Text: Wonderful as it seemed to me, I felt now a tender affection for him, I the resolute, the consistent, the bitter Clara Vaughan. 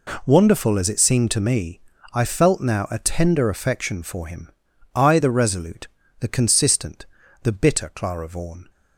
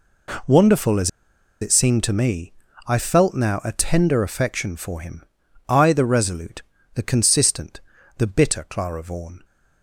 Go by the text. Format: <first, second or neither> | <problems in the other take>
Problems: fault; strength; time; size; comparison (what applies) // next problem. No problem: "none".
first | pauses between "as" and "it"; noticeable; at 1.0 s; 0.52 s long